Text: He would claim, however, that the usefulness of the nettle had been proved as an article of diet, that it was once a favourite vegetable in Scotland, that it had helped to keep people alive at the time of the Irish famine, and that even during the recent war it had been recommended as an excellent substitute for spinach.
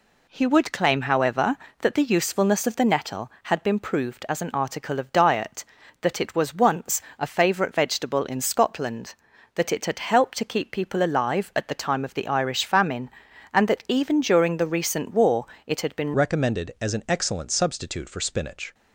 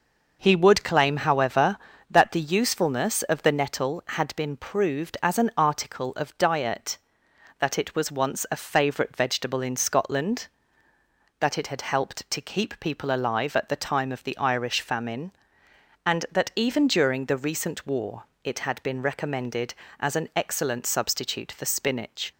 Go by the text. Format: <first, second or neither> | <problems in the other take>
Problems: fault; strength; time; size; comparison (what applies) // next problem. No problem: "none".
second | pauses between "once" and "a"; slight; at 7.0 s; 0.16 s long // pauses between "war" and "it"; slight; at 15.4 s; 0.20 s long; slight in the second // changes voice at "recommended"; from 16.1 s on; 2.6 s long